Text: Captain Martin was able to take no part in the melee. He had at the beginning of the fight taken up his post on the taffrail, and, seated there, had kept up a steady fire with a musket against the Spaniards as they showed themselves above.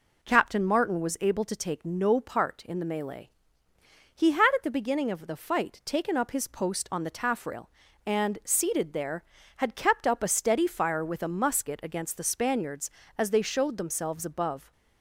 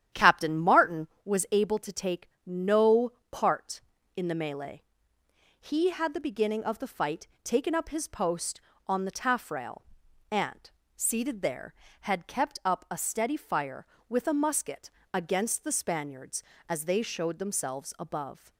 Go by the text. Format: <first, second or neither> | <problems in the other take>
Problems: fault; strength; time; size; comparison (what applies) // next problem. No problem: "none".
first | starts louder than the rest; strong; until 1.3 s; 10 dB // pauses between "take" and "no"; slight; at 2.2 s; 0.16 s long // pauses between "no" and "part"; slight; at 3.1 s; 0.20 s long // skips "at"; at 6.1 s // pauses between "fight" and "taken"; slight; at 7.2 s; 0.16 s long // pauses between "musket" and "against"; slight; at 14.8 s; 0.24 s long